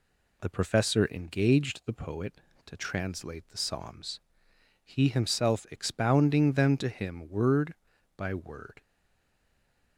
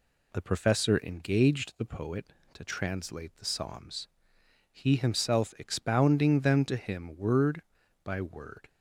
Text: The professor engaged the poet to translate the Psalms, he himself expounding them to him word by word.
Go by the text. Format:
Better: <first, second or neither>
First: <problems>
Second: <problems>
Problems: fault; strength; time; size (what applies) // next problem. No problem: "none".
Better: second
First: stays silent after the last word; noticeable; from 8.8 s on; 1.1 s long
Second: none